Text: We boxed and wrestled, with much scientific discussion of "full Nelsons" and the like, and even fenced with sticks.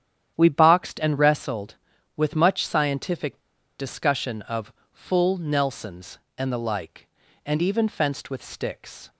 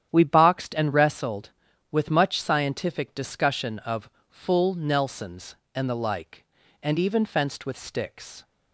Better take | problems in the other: second | starts louder than the rest; strong; until 1.3 s; 10 dB; strong in the second // pauses between "scientific" and "discussion"; at 3.3 s; 0.40 s long // pauses between "of" and "full"; slight; at 4.7 s; 0.18 s long; slight in the second

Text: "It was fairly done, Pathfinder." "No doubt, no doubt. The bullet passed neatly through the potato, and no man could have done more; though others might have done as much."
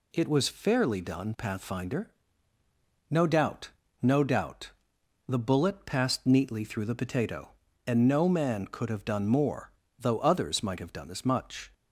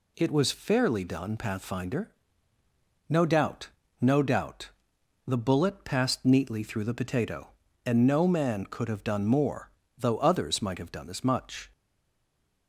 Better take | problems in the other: first | stays silent after the last word; from 11.7 s on; 0.9 s long

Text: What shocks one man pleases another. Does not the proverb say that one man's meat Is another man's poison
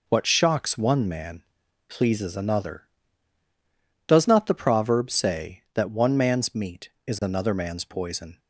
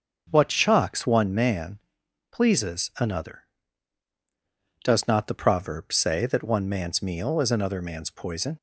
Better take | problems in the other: first | starts louder than the rest; until 1.3 s; 6.5 dB // pauses between "man" and "pleases"; noticeable; at 1.7 s; 0.54 s long; noticeable in the first // says "meal" for "meat"; at 7.0 s

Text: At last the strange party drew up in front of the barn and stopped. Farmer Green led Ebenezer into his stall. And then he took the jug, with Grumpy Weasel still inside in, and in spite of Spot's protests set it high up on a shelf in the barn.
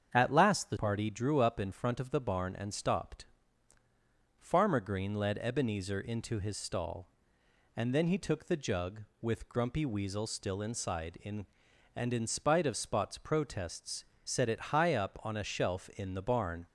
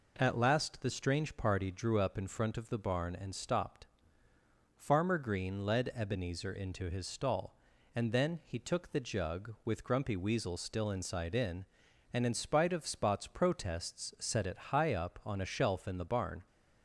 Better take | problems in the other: second | starts louder than the rest; strong; until 1.1 s; 7.5 dB // skips "strange"; at 0.7 s // pauses between "protests" and "set"; slight; at 14.0 s; 0.18 s long

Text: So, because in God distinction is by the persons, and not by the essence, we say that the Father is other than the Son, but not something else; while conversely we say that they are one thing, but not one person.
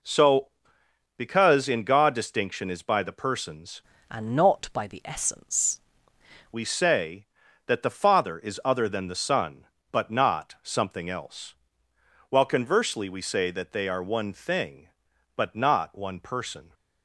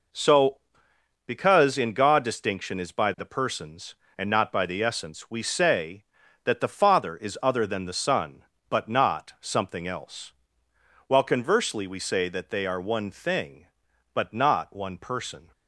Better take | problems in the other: second | changes voice from "and" to "essence"; from 4.0 to 5.8 s; 1.8 s long

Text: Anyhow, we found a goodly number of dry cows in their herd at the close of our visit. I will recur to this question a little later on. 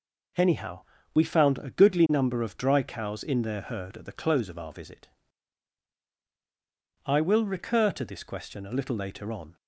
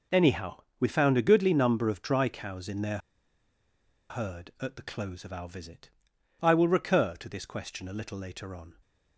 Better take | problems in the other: first | pauses between "their" and "herd"; at 2.9 s; 1.1 s long

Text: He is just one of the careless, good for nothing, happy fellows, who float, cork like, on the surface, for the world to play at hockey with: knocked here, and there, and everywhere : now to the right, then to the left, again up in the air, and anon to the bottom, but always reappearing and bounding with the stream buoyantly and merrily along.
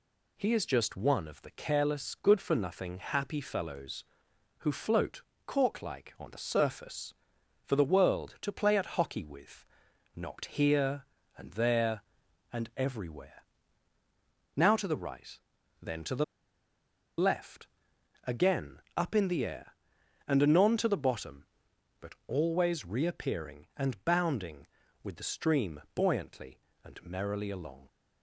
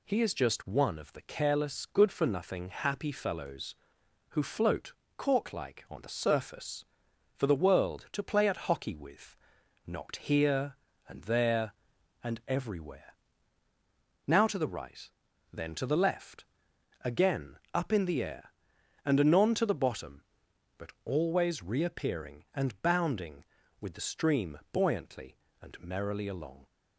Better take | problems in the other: second | pauses between "the" and "left"; noticeable; at 16.2 s; 0.94 s long // pauses between "again" and "up"; slight; at 18.7 s; 0.16 s long; slight in the second

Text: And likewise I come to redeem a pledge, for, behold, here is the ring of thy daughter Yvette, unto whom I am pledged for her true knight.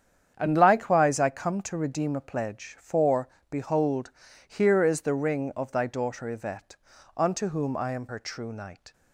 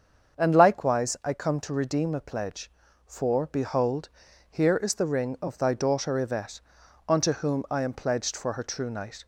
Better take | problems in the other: second | starts louder than the rest; strong; until 1.3 s; 8.5 dB; also in the second // skips "pledged for"; at 8.0 s

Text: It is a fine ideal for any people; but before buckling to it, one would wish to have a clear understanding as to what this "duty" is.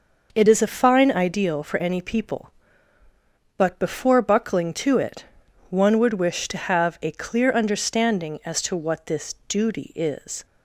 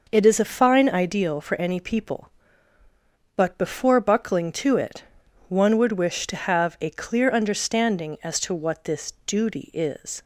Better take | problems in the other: neither | none

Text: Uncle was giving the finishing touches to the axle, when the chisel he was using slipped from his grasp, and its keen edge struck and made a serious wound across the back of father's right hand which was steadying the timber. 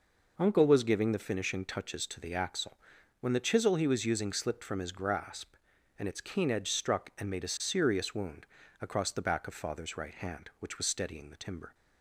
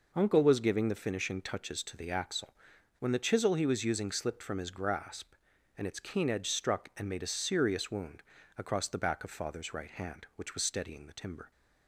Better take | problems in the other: neither | pauses between "wound" and "across"; slight; the same in both

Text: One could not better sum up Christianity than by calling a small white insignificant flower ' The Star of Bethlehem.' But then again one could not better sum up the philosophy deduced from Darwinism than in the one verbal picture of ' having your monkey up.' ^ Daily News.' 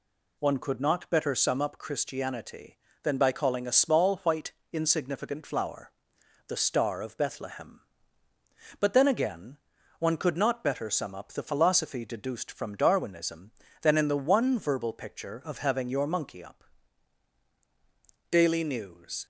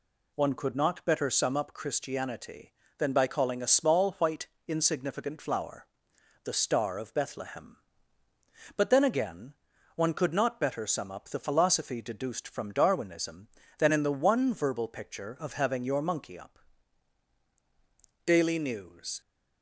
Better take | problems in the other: neither | pauses between "white" and "insignificant"; slight; the same in both // pauses between "again" and "one"; the same in both

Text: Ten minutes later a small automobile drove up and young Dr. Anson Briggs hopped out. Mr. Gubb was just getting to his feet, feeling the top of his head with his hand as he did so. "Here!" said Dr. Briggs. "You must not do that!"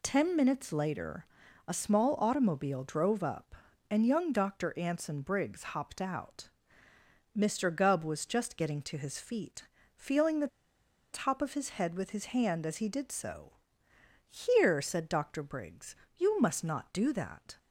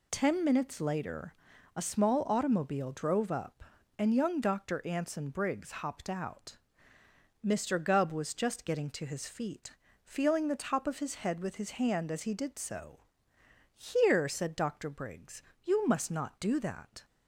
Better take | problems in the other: second | pauses between "later" and "a"; at 1.2 s; 0.42 s long; also in the second // pauses between "the" and "top"; noticeable; at 10.4 s; 0.65 s long

